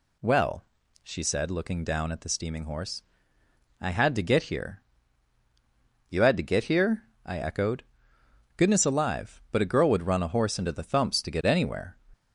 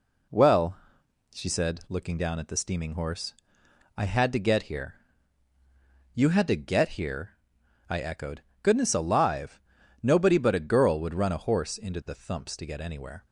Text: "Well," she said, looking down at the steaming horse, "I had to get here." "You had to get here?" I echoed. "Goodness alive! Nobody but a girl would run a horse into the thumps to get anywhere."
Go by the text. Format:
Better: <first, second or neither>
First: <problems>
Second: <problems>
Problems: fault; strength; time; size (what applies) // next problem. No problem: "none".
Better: second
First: skips "Nobody"; at 9.4 s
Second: none